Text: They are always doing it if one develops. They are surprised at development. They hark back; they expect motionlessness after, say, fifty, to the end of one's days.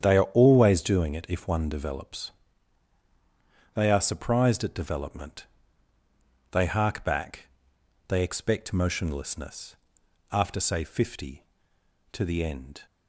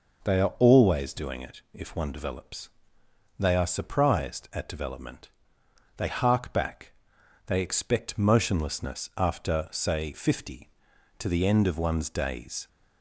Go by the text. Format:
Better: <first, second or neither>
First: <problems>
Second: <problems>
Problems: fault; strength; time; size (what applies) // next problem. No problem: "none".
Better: second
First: starts louder than the rest; strong; until 1.0 s; 9 dB // pauses between "motionlessness" and "after"; noticeable; at 9.7 s; 0.56 s long // stops before "of one's days"; at 12.8 s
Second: none